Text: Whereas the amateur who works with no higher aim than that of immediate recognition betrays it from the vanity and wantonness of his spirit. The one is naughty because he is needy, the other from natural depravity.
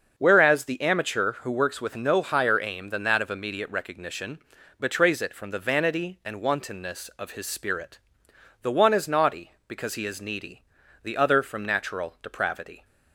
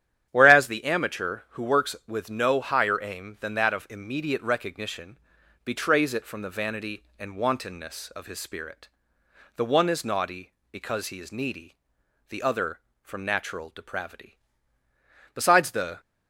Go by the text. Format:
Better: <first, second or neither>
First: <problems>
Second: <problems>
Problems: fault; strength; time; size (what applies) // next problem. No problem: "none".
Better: first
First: starts louder than the rest; until 1.1 s; 6.5 dB // pauses between "recognition" and "betrays"; at 4.3 s; 0.40 s long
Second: starts louder than the rest; strong; until 1.3 s; 10 dB // pauses between "recognition" and "betrays"; noticeable; at 5.1 s; 0.48 s long // goes on to say "Besides the"; noticeable; from 15.3 s on; 0.66 s long